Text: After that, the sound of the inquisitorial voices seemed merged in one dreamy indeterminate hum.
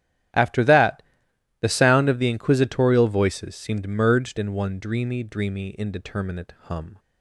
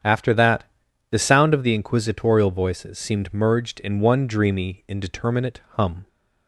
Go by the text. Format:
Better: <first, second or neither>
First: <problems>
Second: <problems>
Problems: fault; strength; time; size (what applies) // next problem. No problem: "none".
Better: second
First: starts louder than the rest; strong; until 1.9 s; 12 dB // says "dreamy" twice; at 5.2 s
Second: starts louder than the rest; strong; until 1.5 s; 8.5 dB